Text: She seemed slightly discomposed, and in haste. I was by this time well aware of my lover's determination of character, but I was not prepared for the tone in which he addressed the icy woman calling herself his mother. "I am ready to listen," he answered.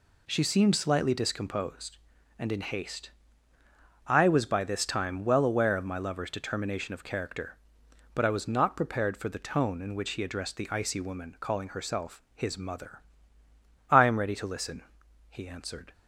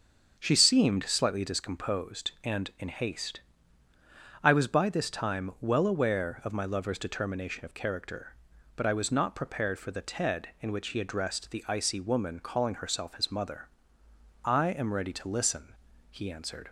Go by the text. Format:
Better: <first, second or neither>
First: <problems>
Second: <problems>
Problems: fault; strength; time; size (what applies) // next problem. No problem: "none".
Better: first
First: none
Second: starts louder than the rest; until 1.4 s; 7 dB // says "ted" for "tone"; at 10.0 s